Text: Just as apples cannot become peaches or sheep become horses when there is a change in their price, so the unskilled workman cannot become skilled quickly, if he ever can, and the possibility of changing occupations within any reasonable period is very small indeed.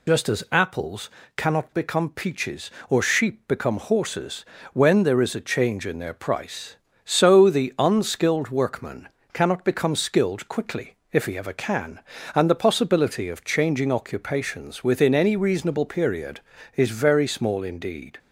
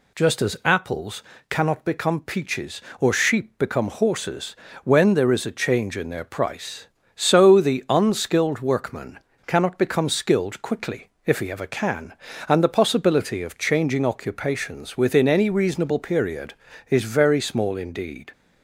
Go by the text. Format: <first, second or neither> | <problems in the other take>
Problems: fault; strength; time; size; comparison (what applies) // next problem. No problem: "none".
second | loses the start of "Just"; at 0.0 s; 50 ms // pauses between "apples" and "cannot"; slight; at 1.0 s; 0.26 s long; slight in the second // pauses between "horses" and "when"; slight; at 4.4 s; 0.28 s long; slight in the second // pauses between "workman" and "cannot"; slight; at 9.0 s; 0.24 s long; slight in the second